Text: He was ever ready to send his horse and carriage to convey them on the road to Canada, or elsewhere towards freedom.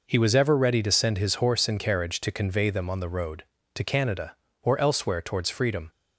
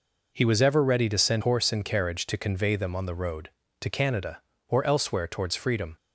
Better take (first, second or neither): first